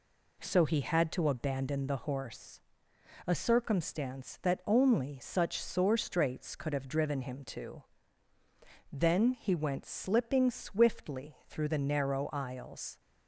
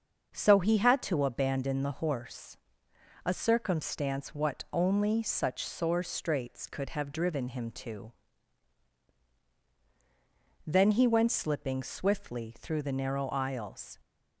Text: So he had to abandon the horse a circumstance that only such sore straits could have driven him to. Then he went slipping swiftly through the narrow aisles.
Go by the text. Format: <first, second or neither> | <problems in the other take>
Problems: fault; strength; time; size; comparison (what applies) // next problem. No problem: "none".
first | starts louder than the rest; until 1.3 s; 6.5 dB // pauses between "horse" and "a"; noticeable; at 2.5 s; 0.70 s long; noticeable in the first // says "what" for "that"; at 4.3 s